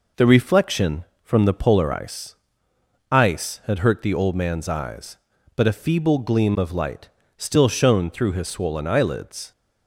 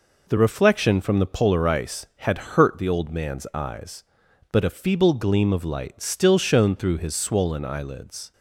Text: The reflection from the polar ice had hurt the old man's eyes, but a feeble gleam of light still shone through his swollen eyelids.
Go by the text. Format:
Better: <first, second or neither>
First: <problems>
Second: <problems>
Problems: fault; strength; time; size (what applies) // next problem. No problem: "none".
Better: second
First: says "ice" twice; at 3.1 s // pauses between "light" and "still"; slight; at 7.0 s; 0.26 s long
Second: none